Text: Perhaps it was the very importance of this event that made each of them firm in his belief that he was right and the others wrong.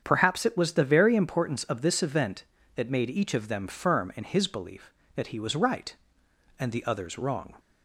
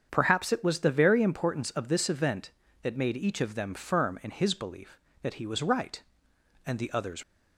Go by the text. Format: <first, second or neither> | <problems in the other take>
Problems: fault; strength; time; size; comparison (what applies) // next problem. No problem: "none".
first | starts louder than the rest; strong; until 1.1 s; 7.5 dB; strong in the first // stops before "wrong"; at 7.2 s